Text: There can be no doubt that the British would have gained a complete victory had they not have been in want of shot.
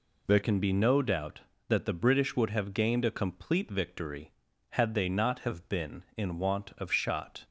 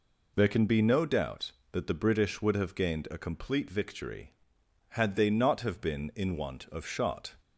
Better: second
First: changes voice at "can"; from 0.4 s on; 7.0 s long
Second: none

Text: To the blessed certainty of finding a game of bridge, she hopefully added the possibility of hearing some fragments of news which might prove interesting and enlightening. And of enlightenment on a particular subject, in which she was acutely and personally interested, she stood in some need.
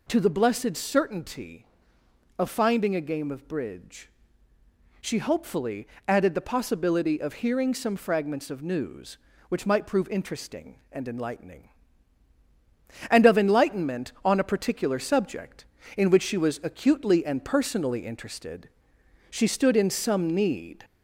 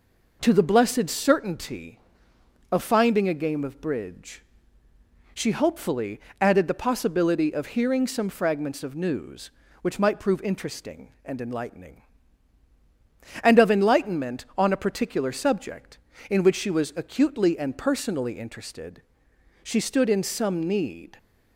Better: second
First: gets louder; slight; throughout; 2 dB // pauses between "hopefully" and "added"; slight; at 5.8 s; 0.20 s long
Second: pauses between "hopefully" and "added"; slight; at 6.1 s; 0.20 s long

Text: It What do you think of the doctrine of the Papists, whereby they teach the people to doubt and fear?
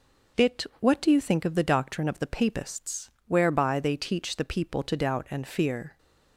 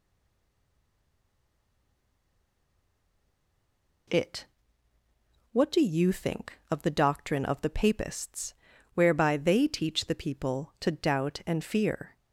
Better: first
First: none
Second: stays silent before the first word; strong; until 4.0 s; 4.0 s long // pauses between "It" and "What"; at 4.4 s; 1.0 s long

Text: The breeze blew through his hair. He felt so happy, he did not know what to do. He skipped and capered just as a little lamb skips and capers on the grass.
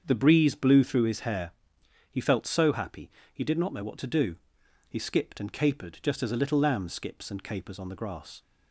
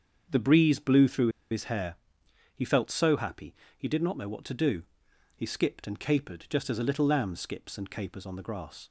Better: first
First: starts louder than the rest; strong; until 1.0 s; 7 dB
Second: starts louder than the rest; strong; until 1.5 s; 7 dB // pauses between "through" and "his"; slight; at 1.2 s; 0.22 s long

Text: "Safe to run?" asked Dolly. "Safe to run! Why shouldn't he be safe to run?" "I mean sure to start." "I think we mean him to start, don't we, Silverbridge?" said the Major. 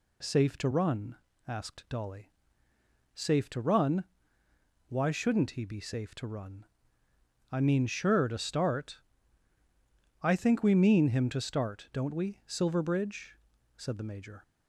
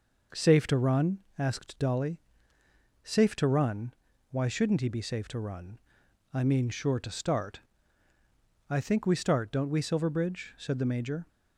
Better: first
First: none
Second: skips "mean him to"; at 9.1 s

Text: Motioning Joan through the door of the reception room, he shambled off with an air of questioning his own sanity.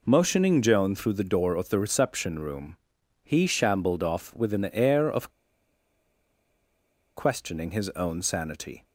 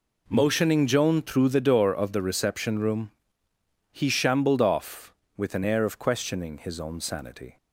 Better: second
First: pauses between "of" and "questioning"; strong; at 5.3 s; 1.8 s long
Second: none

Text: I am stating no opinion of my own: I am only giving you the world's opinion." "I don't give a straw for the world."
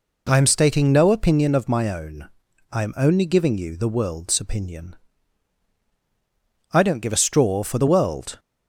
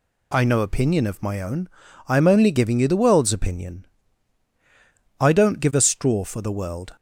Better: first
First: none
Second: skips "am stating"; at 0.4 s

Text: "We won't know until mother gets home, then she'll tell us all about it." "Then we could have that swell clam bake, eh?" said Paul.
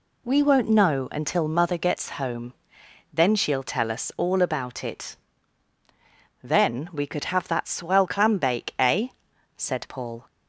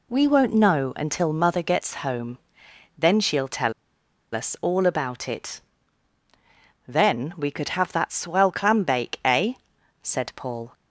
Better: first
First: none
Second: pauses between "tell" and "us"; noticeable; at 3.7 s; 0.62 s long

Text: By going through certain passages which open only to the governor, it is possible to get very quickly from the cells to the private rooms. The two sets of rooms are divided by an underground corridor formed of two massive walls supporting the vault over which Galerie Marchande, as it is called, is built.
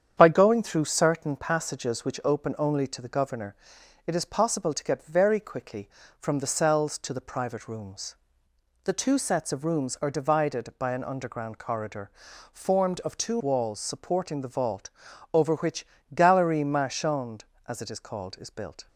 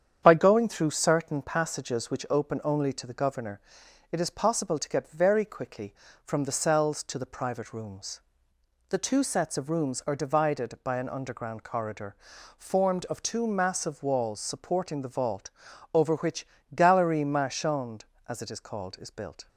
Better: second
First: starts louder than the rest; strong; until 1.1 s; 8.5 dB // pauses between "corridor" and "formed"; at 12.1 s; 0.42 s long // skips "massive"; at 13.4 s // pauses between "vault" and "over"; at 14.8 s; 0.44 s long // pauses between "which" and "Galerie"; slight; at 15.8 s; 0.28 s long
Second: starts louder than the rest; strong; until 1.2 s; 8.5 dB // pauses between "corridor" and "formed"; at 12.1 s; 0.42 s long // pauses between "vault" and "over"; at 15.4 s; 0.44 s long // pauses between "which" and "Galerie"; slight; at 16.4 s; 0.28 s long

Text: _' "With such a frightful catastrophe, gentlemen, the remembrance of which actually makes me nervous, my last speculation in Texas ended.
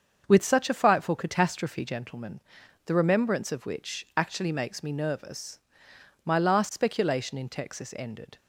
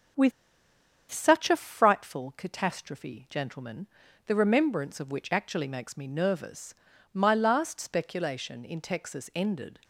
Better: first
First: starts louder than the rest; until 1.2 s; 7 dB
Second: starts louder than the rest; strong; until 1.9 s; 7.5 dB // pauses between "With" and "such"; noticeable; at 0.3 s; 0.79 s long

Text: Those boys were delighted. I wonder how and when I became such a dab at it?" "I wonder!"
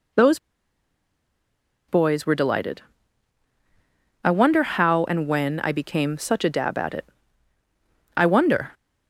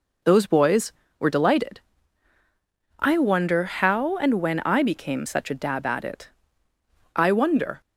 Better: second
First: pauses between "Those" and "boys"; strong; at 0.3 s; 1.5 s long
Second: none

